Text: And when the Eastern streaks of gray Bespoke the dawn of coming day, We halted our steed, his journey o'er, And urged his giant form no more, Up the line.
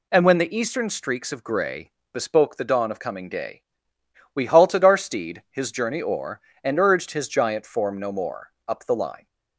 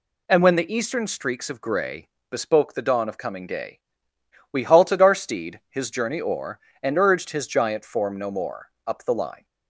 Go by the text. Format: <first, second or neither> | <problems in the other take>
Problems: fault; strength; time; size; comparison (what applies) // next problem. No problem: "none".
neither | pauses between "gray" and "Bespoke"; slight; the same in both